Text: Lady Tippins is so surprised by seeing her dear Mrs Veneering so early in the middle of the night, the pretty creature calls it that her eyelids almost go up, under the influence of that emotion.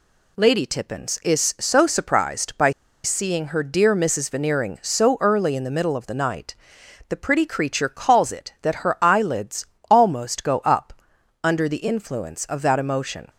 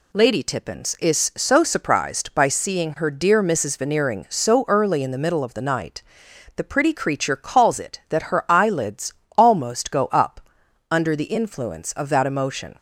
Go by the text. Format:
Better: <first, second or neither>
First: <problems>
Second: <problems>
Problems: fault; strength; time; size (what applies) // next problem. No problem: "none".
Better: second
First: pauses between "by" and "seeing"; slight; at 2.7 s; 0.31 s long // pauses between "eyelids" and "almost"; slight; at 9.6 s; 0.26 s long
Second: pauses between "eyelids" and "almost"; slight; at 9.1 s; 0.26 s long